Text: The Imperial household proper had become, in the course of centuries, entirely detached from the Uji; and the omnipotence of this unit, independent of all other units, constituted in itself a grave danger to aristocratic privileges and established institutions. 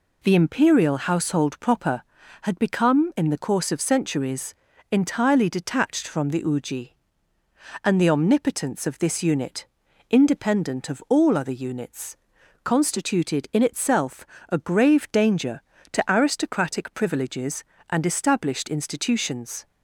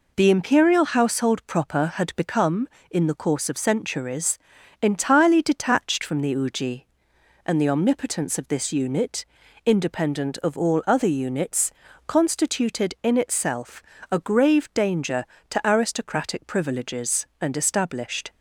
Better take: first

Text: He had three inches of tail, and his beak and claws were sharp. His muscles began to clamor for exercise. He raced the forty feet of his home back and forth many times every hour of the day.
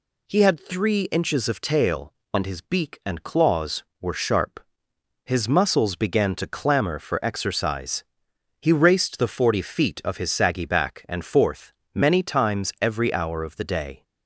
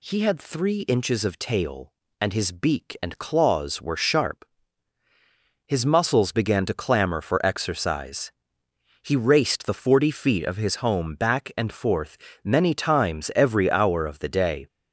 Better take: second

